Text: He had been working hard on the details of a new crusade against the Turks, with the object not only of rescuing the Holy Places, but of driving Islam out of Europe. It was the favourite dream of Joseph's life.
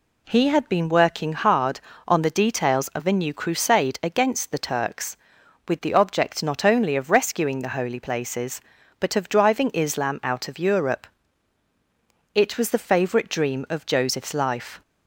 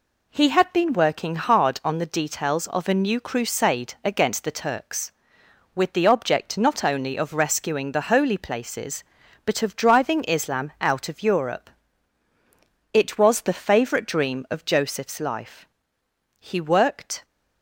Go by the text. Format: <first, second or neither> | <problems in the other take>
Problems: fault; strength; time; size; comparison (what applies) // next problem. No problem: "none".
first | goes on to say "He worked"; noticeable; from 16.3 s on; 0.86 s long